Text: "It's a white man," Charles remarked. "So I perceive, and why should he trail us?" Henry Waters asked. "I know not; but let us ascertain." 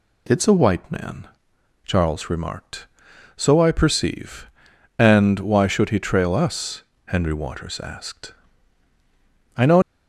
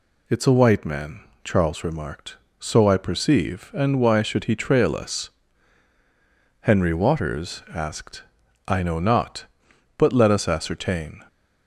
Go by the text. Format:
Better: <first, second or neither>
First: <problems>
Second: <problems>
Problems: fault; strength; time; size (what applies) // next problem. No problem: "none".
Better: second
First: stops before "not but let us ascertain"; at 9.8 s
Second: none